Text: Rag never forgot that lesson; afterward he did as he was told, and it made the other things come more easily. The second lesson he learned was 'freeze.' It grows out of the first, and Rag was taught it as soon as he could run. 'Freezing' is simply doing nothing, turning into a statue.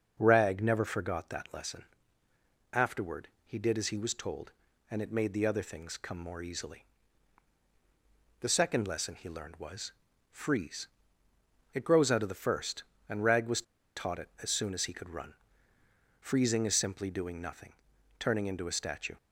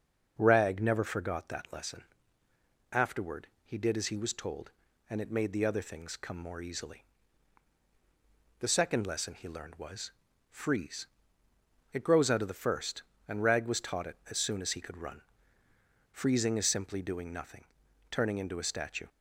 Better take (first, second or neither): second